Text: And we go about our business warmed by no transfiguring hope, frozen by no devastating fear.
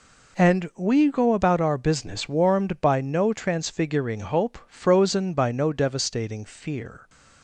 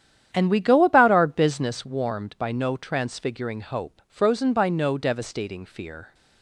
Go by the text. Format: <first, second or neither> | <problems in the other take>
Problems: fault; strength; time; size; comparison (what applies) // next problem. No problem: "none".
first | starts louder than the rest; strong; until 1.7 s; 10 dB